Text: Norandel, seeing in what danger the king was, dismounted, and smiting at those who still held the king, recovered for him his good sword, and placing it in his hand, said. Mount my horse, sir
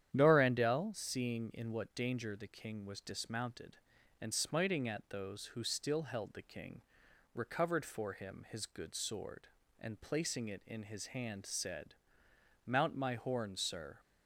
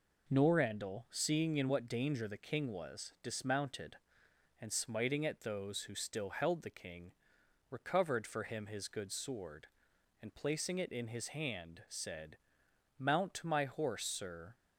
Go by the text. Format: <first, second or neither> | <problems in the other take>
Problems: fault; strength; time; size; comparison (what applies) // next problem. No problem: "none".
second | starts louder than the rest; strong; until 1.1 s; 10 dB // says "horn" for "horse"; at 13.1 s